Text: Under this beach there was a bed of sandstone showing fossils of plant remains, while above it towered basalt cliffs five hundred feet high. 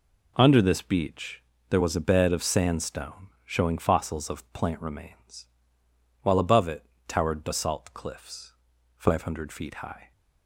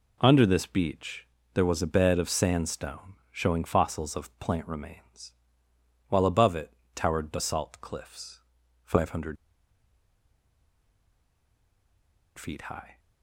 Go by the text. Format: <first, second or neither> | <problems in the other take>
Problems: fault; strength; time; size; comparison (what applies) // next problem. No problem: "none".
first | pauses between "beach" and "there"; slight; at 1.2 s; 0.26 s long; slight in the first // pauses between "sandstone" and "showing"; slight; at 3.1 s; 0.18 s long; slight in the first // pauses between "it" and "towered"; slight; at 6.7 s; 0.20 s long; slight in the first // pauses between "cliffs" and "five"; at 8.4 s; 0.42 s long; also in the first // pauses between "hundred" and "feet"; strong; at 9.3 s; 3.0 s long